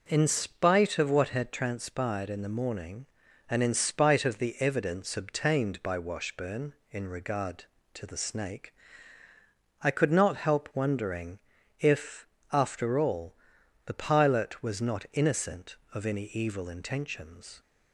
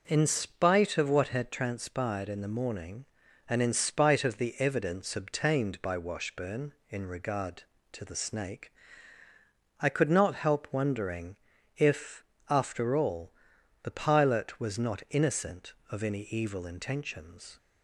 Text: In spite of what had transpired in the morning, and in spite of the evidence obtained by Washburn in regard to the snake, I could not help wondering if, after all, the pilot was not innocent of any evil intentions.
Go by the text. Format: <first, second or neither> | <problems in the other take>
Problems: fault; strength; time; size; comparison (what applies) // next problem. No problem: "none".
neither | pauses between "wondering" and "if"; the same in both